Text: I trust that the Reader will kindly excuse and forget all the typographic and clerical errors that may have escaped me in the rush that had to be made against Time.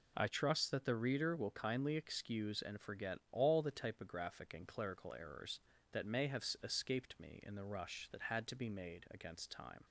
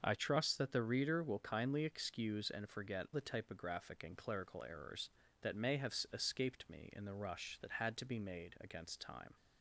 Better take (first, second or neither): first